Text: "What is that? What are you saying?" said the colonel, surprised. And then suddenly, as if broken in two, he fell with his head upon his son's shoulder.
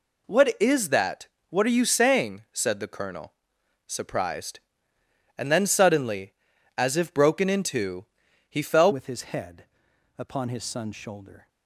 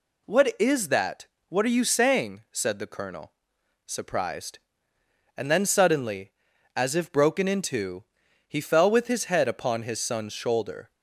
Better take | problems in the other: second | changes voice at "with"; from 8.9 s on; 2.5 s long // pauses between "head" and "upon"; noticeable; at 9.6 s; 0.54 s long

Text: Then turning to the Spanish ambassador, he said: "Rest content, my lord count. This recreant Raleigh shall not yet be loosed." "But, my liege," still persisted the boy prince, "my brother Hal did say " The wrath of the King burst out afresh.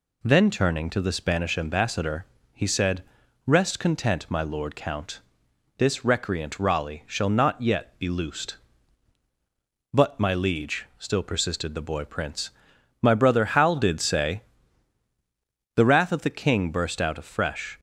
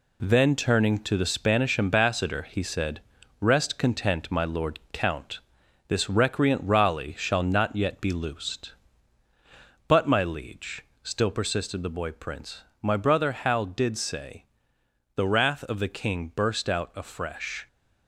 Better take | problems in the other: neither | none

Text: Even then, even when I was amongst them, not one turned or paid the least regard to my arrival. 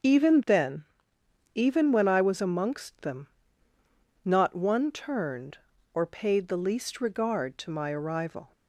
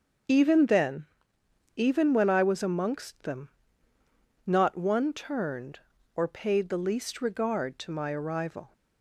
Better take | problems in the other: neither | starts louder than the rest; the same in both

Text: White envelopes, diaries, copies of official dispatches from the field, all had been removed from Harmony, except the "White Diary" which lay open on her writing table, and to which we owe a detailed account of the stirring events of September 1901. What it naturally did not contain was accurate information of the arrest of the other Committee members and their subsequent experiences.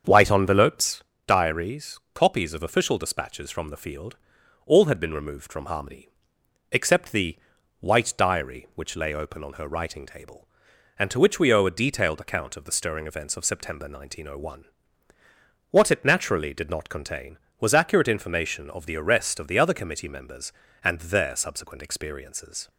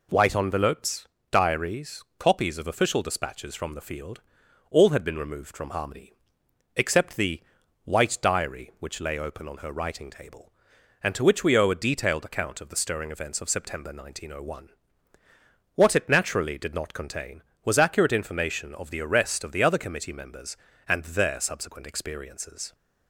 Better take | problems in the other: second | starts louder than the rest; until 1.2 s; 7 dB // pauses between "the" and "White"; at 7.3 s; 0.40 s long; also in the second

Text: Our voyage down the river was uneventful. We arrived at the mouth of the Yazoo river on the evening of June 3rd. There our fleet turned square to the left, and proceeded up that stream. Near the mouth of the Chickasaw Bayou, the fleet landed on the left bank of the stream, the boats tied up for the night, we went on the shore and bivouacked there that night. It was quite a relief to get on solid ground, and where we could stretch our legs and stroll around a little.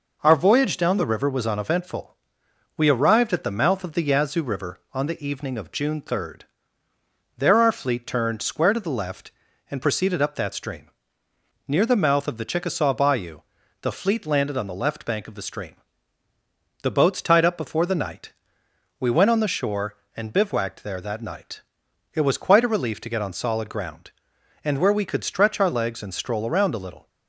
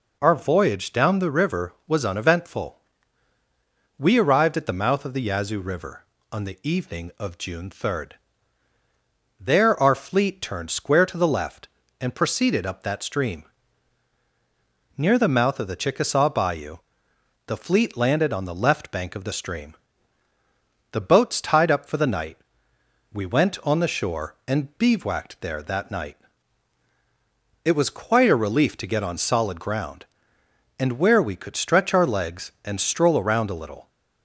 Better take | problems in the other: second | says "before" for "for"; at 17.5 s

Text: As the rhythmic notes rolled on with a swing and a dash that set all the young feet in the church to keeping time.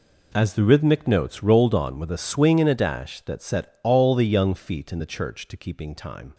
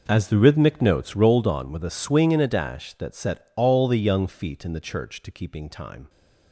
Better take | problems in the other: first | starts louder than the rest; noticeable; until 1.3 s; 5.5 dB

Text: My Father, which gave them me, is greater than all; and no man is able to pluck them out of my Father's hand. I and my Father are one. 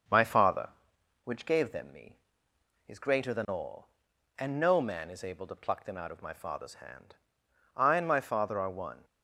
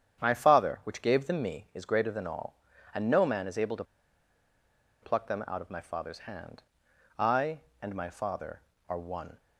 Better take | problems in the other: first | starts louder than the rest; strong; until 1.2 s; 8.5 dB; also in the first // pauses between "to" and "pluck"; at 3.8 s; 1.1 s long

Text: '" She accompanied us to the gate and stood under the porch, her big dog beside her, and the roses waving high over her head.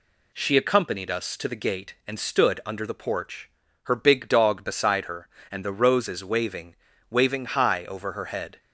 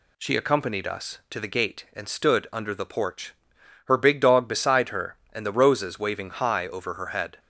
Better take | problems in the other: second | says "waving" twice; at 7.1 s

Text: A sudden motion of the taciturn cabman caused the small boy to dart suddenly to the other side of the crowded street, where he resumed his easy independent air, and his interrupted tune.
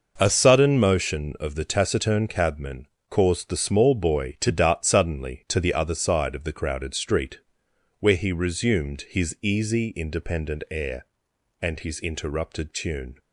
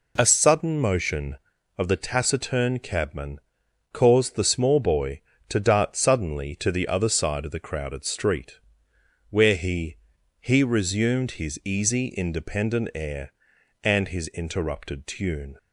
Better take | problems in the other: first | pauses between "cabman" and "caused"; noticeable; at 3.3 s; 0.56 s long; slight in the first // says "he" twice; at 10.4 s

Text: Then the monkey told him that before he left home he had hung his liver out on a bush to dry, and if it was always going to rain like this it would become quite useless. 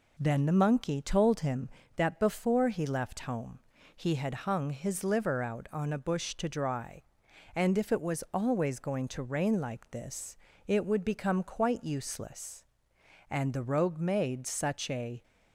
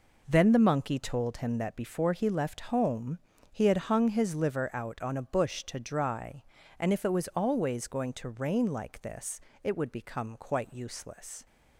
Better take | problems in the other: second | pauses between "home" and "he"; slight; at 3.5 s; 0.36 s long; slight in the second // pauses between "this" and "it"; slight; at 10.3 s; 0.30 s long; slight in the second // goes on to say "And the rogue made such a"; strong; from 13.2 s on; 1.9 s long

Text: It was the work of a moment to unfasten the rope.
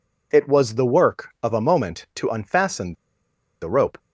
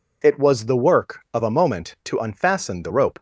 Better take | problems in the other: second | pauses between "unfasten" and "the"; noticeable; at 2.9 s; 0.67 s long

